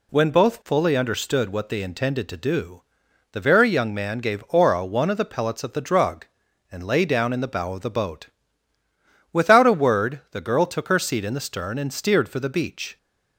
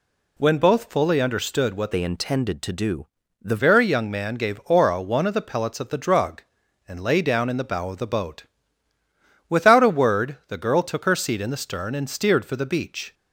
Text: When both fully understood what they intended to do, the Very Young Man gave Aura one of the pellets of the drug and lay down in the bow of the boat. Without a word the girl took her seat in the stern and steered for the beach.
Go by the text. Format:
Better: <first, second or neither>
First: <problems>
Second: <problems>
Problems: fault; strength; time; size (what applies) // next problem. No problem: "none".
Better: first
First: none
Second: changes voice from "they" to "the"; from 1.9 to 3.5 s; 1.6 s long